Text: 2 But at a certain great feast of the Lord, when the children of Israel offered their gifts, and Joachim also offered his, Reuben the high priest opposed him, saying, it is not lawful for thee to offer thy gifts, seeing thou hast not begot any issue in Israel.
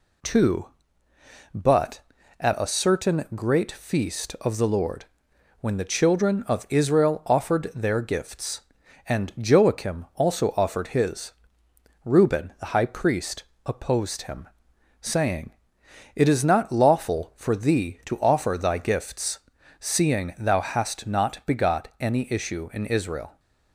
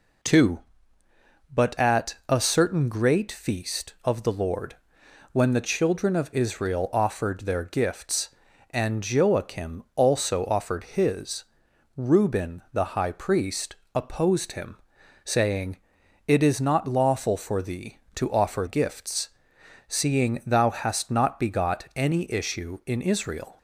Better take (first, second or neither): first